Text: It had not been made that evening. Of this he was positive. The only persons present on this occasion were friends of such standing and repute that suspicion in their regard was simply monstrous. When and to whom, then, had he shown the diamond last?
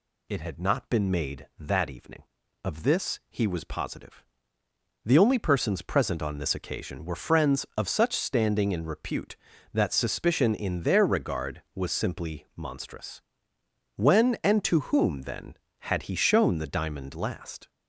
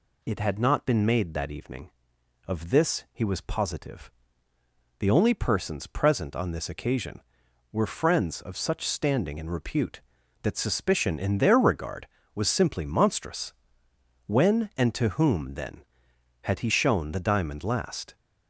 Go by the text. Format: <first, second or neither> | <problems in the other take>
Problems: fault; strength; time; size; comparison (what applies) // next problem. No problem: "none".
neither | none